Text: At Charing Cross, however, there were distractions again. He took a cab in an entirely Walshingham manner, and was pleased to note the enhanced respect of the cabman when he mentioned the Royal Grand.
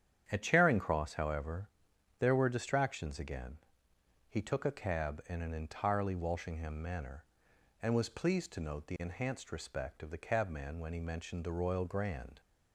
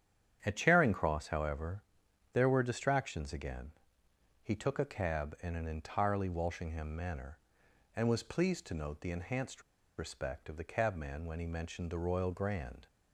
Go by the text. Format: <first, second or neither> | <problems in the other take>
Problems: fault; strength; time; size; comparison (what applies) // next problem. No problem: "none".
first | starts louder than the rest; strong; until 1.4 s; 9 dB; strong in the first // pauses between "enhanced" and "respect"; at 9.6 s; 0.36 s long